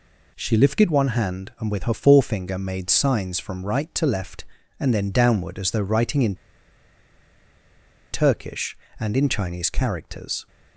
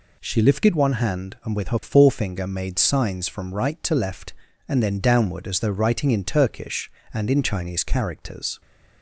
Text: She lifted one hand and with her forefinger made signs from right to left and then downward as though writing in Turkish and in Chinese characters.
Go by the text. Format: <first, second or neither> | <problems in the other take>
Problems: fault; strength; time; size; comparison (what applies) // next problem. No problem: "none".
second | pauses between "in" and "Turkish"; strong; at 6.3 s; 1.7 s long